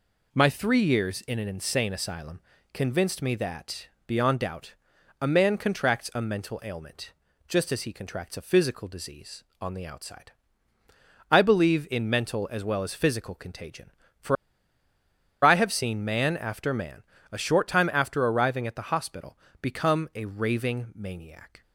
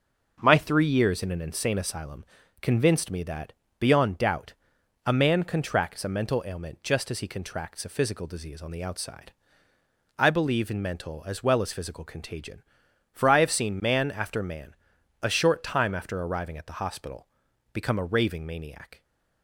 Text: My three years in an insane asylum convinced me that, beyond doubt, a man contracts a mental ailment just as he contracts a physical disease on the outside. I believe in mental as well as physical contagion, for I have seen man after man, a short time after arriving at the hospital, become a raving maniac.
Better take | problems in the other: second | pauses between "asylum" and "convinced"; slight; at 2.3 s; 0.34 s long; also in the second // pauses between "ailment" and "just"; slight; at 7.1 s; 0.36 s long // pauses between "for" and "I"; at 14.3 s; 1.0 s long

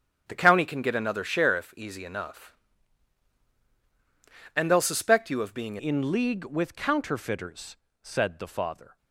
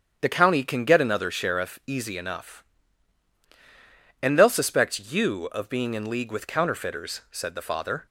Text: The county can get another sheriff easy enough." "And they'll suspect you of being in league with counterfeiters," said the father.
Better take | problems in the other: second | starts louder than the rest; strong; until 1.2 s; 9 dB; strong in the second // changes voice at "in"; from 5.7 s on; 3.2 s long

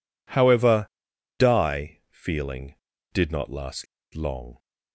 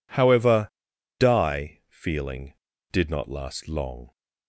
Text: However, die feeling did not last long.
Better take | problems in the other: second | pauses between "last" and "long"; slight; at 3.8 s; 0.28 s long

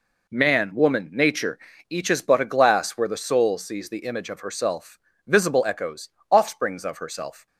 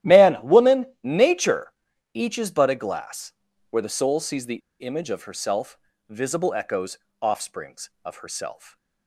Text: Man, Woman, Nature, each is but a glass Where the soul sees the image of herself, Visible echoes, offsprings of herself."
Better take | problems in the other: first | starts louder than the rest; strong; until 1.2 s; 13 dB // pauses between "glass" and "Where"; slight; at 3.3 s; 0.36 s long // pauses between "the" and "image"; slight; at 4.6 s; 0.22 s long

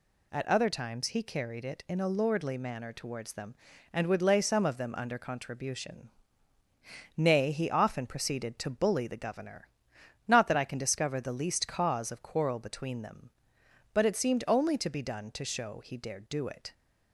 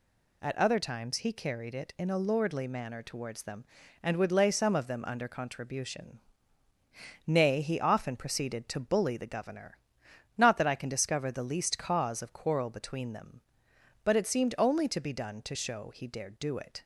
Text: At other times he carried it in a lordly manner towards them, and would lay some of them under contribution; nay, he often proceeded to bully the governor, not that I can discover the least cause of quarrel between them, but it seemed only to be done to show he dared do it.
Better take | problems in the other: neither | none

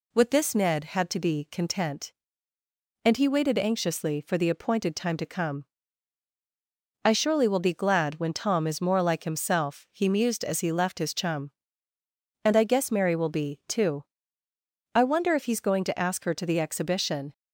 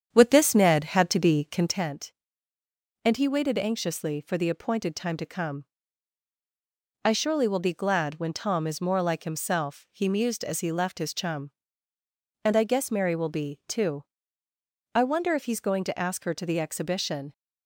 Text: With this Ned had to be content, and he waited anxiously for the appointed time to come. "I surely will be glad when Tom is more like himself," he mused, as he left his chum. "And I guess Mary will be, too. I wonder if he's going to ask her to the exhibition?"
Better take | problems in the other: first | starts louder than the rest; strong; until 1.9 s; 8.5 dB

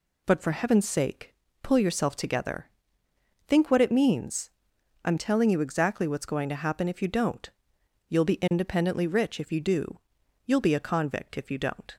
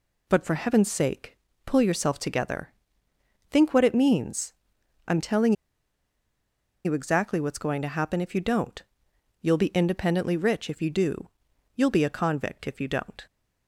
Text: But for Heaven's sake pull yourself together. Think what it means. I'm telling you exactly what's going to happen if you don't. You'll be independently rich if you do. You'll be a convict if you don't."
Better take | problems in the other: first | pauses between "sake" and "pull"; slight; at 1.3 s; 0.30 s long; slight in the first // pauses between "telling" and "you"; strong; at 5.5 s; 1.3 s long

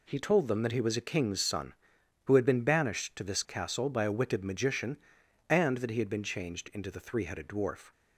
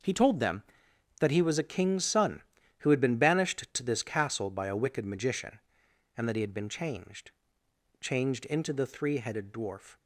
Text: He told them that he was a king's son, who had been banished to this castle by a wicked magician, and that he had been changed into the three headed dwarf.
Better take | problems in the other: first | starts louder than the rest; noticeable; until 1.6 s; 6 dB // says "changed" twice; at 8.0 s

